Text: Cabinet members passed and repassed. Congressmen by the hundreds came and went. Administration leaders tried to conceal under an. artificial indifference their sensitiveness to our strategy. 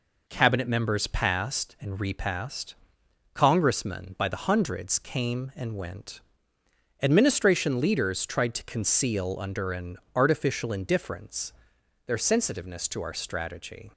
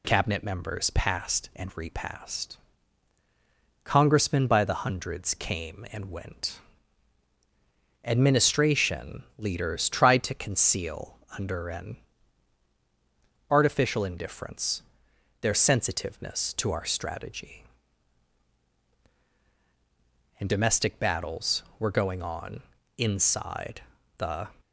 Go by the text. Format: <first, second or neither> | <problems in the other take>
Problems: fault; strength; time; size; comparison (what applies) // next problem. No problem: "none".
first | pauses between "conceal" and "under"; slight; at 11.1 s; 0.20 s long // pauses between "indifference" and "their"; noticeable; at 14.8 s; 0.60 s long; noticeable in the first // goes on to say "And domestic battles were going on inside the"; strong; from 20.3 s on; 4.0 s long